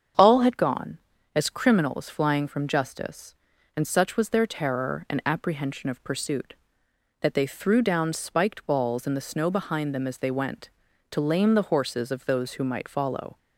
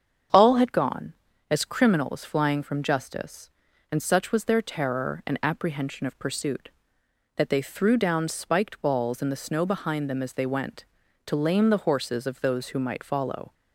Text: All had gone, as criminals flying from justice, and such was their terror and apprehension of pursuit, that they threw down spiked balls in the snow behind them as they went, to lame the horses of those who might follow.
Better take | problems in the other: neither | starts louder than the rest; strong; the same in both

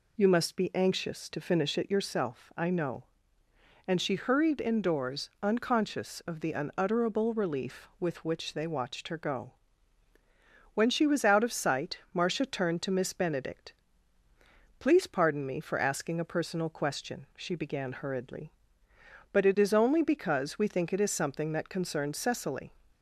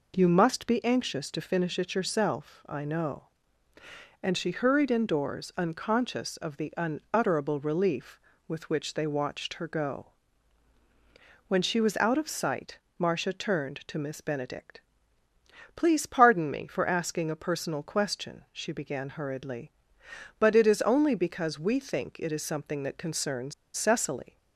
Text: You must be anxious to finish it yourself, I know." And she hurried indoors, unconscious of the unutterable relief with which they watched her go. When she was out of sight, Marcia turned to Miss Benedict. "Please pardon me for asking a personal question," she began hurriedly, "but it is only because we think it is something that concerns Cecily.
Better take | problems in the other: first | pauses between "concerns" and "Cecily"; slight; at 23.5 s; 0.23 s long

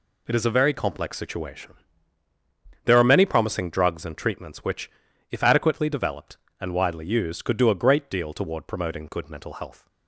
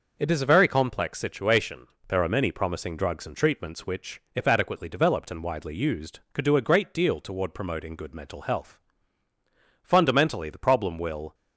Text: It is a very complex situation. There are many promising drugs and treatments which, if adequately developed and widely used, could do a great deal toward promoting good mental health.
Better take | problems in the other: first | goes on to say "Fundamentally the problem will"; from 9.8 s on; 1.5 s long

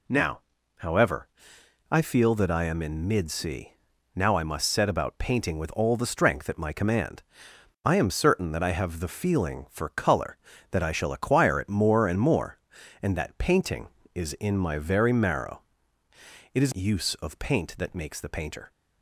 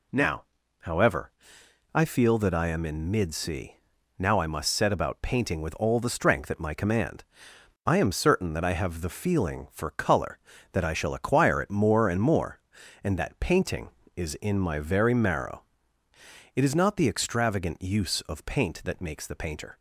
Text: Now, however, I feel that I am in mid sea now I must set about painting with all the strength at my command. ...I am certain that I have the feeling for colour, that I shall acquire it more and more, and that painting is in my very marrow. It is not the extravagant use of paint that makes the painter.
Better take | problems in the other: second | pauses between "sea" and "now"; noticeable; at 3.7 s; 0.46 s long; noticeable in the second // skips "not the extravagant"; at 16.7 s

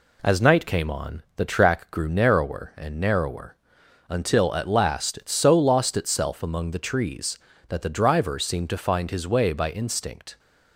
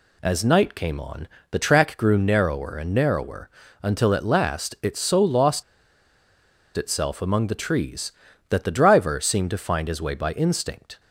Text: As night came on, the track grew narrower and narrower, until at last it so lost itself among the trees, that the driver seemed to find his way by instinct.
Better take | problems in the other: first | pauses between "lost" and "itself"; at 5.6 s; 1.1 s long

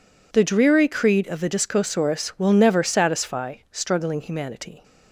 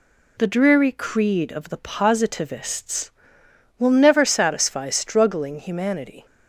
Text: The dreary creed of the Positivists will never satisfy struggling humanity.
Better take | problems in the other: second | says "Discosaurus" for "Positivists"; at 1.4 s

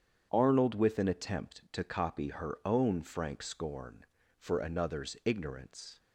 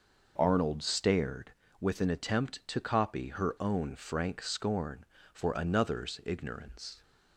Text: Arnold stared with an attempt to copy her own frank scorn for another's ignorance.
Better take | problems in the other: second | starts louder than the rest; strong; until 1.3 s; 8 dB // skips "stared"; at 0.7 s

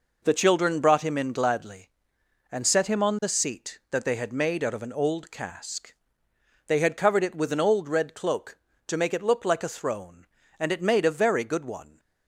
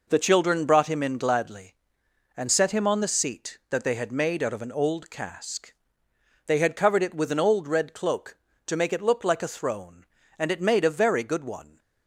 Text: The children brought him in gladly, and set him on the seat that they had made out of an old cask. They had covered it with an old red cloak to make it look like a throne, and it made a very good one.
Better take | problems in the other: neither | none

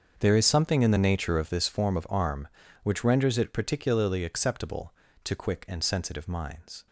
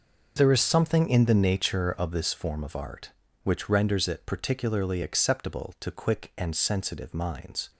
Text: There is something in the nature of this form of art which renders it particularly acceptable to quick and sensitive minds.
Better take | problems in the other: second | starts louder than the rest; until 1.1 s; 7 dB // says "arm" for "art"; at 2.0 s

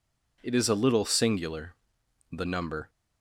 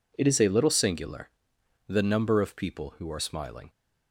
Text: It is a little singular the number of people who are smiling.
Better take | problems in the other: second | pauses between "singular" and "the"; noticeable; at 1.7 s; 0.58 s long; noticeable in the second // stops before "of people who are smiling"; at 2.8 s

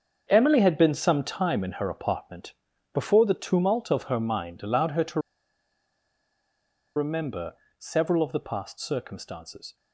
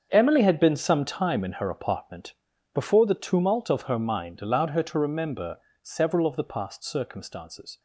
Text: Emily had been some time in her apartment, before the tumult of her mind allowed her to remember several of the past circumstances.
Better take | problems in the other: second | starts louder than the rest; until 1.2 s; 7 dB; strong in the second // pauses between "to" and "remember"; strong; at 5.2 s; 1.7 s long // pauses between "remember" and "several"; slight; at 7.5 s; 0.24 s long; slight in the second

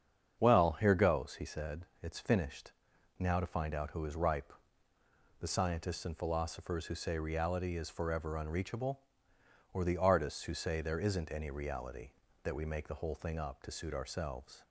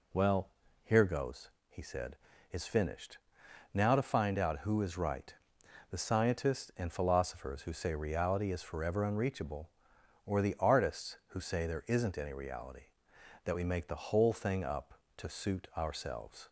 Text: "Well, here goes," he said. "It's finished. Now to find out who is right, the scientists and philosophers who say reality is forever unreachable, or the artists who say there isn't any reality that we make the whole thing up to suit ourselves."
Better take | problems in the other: second | starts louder than the rest; strong; until 1.4 s; 7.5 dB // says "ripe" for "right"; at 4.1 s

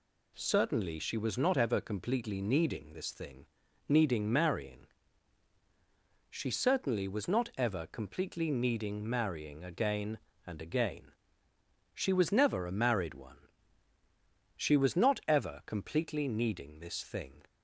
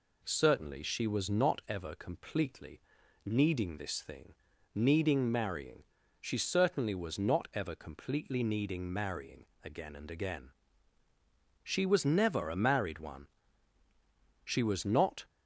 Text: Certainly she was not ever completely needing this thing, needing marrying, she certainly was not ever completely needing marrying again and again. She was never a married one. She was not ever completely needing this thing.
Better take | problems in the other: first | pauses between "completely" and "needing"; at 2.8 s; 0.44 s long // pauses between "marrying" and "again"; slight; at 9.4 s; 0.18 s long // stops before "ever completely needing this thing"; at 15.2 s

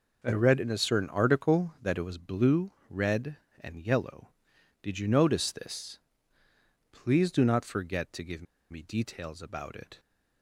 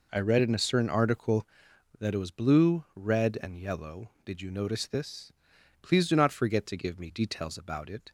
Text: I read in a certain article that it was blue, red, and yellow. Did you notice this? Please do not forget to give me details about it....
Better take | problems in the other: second | pauses between "give" and "me"; slight; at 8.4 s; 0.27 s long

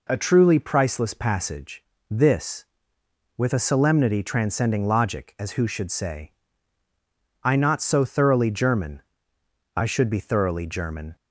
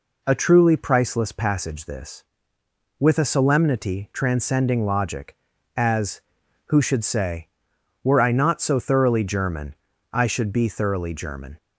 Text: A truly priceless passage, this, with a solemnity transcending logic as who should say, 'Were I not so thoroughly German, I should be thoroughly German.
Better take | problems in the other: second | skips "Were"; at 6.8 s

